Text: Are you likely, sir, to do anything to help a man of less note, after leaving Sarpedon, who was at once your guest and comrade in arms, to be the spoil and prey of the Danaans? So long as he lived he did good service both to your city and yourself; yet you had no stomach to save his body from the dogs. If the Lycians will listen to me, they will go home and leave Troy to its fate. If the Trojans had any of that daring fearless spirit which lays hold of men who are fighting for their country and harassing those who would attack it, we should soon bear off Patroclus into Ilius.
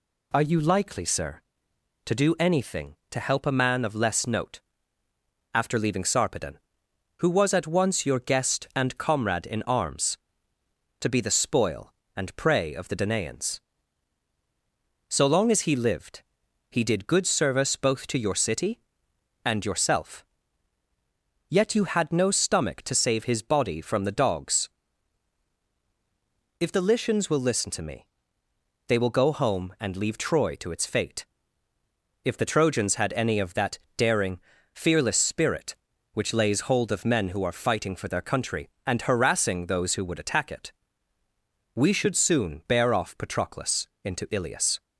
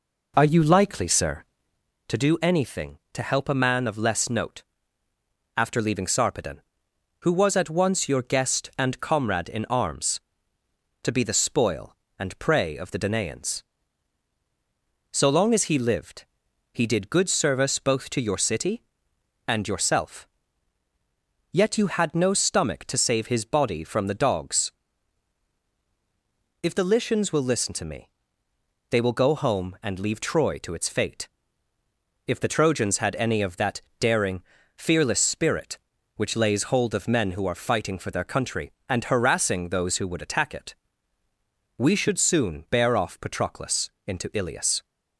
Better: first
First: pauses between "lived" and "he"; noticeable; at 16.2 s; 0.48 s long // pauses between "that" and "daring"; slight; at 33.7 s; 0.18 s long // pauses between "daring" and "fearless"; slight; at 34.4 s; 0.34 s long // pauses between "Patroclus" and "into"; slight; at 43.8 s; 0.18 s long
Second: starts louder than the rest; noticeable; until 1.8 s; 4 dB // pauses between "lived" and "he"; noticeable; at 16.2 s; 0.48 s long // pauses between "that" and "daring"; slight; at 33.8 s; 0.18 s long // pauses between "daring" and "fearless"; slight; at 34.4 s; 0.34 s long // pauses between "Patroclus" and "into"; slight; at 43.8 s; 0.18 s long

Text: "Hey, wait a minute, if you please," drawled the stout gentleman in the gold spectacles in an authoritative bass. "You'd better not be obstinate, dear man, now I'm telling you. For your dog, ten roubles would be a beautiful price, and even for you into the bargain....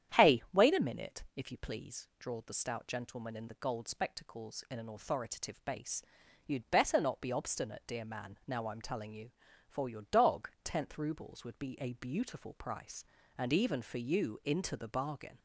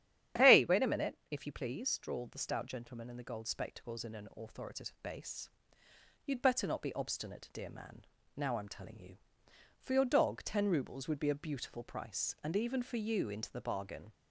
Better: second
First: starts louder than the rest; strong; until 1.3 s; 9.5 dB // says "tenth" for "ten"; at 10.6 s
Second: starts louder than the rest; strong; until 1.5 s; 10.5 dB

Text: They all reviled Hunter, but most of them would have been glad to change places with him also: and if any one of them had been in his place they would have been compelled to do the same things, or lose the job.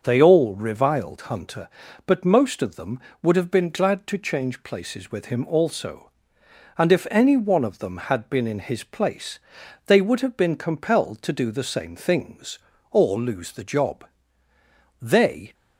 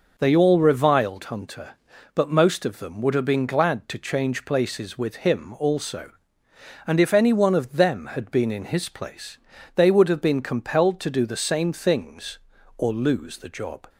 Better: second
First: starts louder than the rest; until 1.0 s; 6.5 dB // pauses between "place" and "they"; noticeable; at 9.3 s; 0.48 s long // goes on to say "They"; from 14.9 s on; 0.54 s long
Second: pauses between "place" and "they"; at 9.3 s; 0.38 s long

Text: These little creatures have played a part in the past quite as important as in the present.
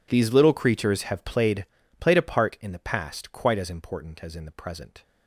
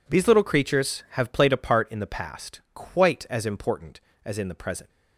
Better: second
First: says "played" twice; at 1.9 s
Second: none

